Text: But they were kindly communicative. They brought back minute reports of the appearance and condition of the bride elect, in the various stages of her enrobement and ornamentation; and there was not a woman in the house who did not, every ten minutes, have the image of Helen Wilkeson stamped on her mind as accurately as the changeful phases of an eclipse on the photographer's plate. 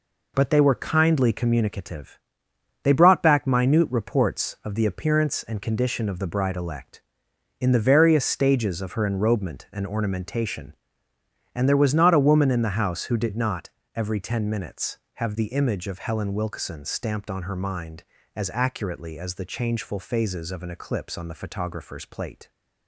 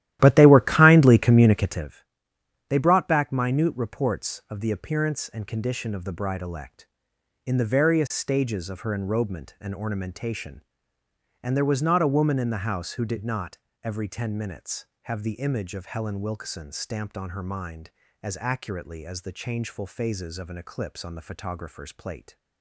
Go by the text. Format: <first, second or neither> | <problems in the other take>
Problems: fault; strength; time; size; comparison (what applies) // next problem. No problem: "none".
first | starts louder than the rest; strong; until 1.9 s; 13.5 dB